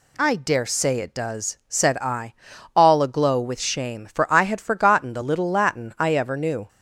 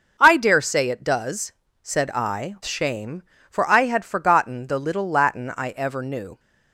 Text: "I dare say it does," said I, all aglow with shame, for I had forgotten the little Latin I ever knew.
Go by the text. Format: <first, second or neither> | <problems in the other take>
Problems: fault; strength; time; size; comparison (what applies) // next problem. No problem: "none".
first | skips "all aglow with"; at 2.6 s